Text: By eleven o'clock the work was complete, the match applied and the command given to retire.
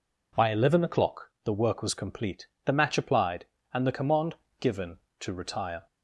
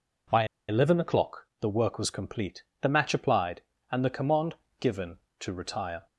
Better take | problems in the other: first | pauses between "By" and "eleven"; slight; at 0.4 s; 0.23 s long // pauses between "command" and "given"; slight; at 4.5 s; 0.24 s long; slight in the first

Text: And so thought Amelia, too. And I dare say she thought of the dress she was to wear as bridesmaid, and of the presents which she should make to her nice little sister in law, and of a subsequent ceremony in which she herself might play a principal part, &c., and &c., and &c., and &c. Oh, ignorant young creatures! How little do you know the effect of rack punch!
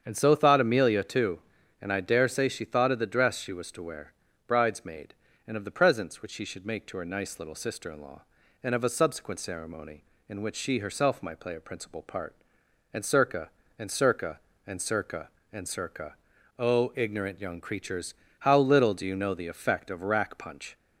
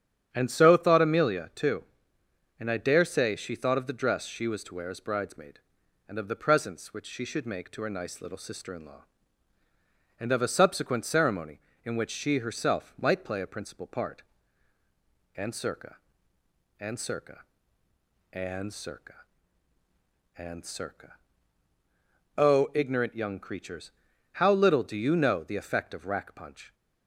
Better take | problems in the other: second | starts louder than the rest; strong; until 1.0 s; 7.5 dB; strong in the second // skips "as"; at 4.2 s

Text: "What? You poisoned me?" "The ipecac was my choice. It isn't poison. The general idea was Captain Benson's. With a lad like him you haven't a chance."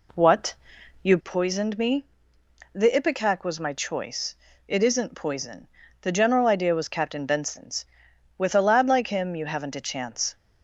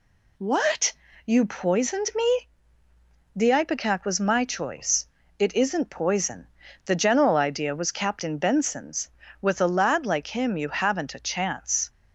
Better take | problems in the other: second | starts louder than the rest; slight; until 1.4 s; 2.5 dB

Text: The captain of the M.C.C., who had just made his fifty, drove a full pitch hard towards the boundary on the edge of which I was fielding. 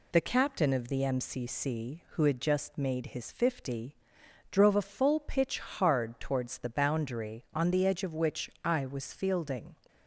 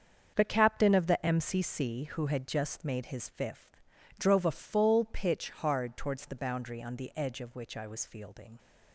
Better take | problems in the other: first | starts louder than the rest; until 1.3 s; 7 dB // says "fifth" for "fifty"; at 3.2 s

